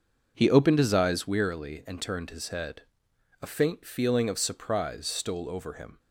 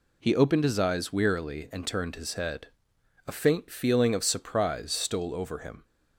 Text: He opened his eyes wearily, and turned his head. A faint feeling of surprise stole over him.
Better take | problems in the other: second | starts louder than the rest; noticeable; until 1.3 s; 6 dB

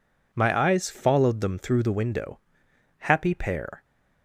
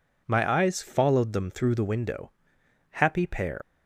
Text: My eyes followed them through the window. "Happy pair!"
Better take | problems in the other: first | leaves "pair" unfinished; at 3.6 s; 140 ms

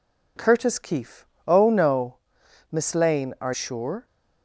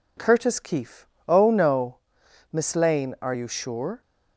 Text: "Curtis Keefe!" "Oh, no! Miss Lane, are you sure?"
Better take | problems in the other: second | skips "you"; at 3.5 s

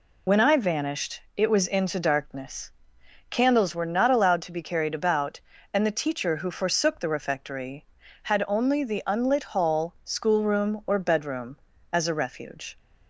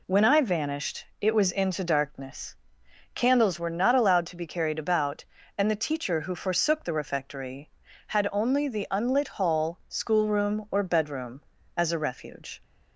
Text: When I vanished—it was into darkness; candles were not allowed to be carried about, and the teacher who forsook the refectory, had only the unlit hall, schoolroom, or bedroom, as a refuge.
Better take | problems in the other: second | loses the start of "When"; at 0.2 s; 55 ms

